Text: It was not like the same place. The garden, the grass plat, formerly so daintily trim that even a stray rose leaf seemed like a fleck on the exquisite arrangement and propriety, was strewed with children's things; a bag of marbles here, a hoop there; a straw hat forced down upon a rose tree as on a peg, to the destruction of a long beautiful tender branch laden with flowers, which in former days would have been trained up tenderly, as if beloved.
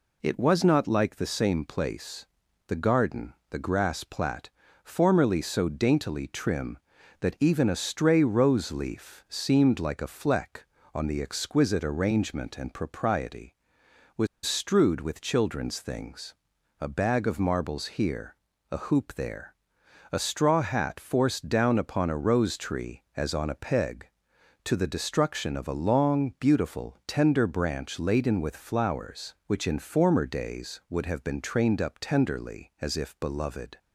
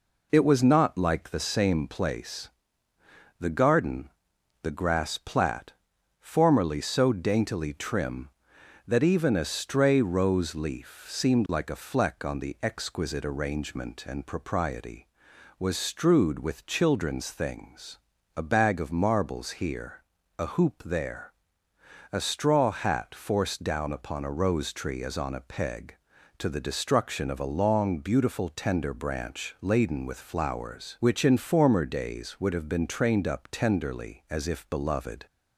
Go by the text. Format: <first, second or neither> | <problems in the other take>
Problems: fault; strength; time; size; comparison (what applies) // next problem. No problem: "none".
second | pauses between "was" and "strewed"; slight; at 14.2 s; 0.18 s long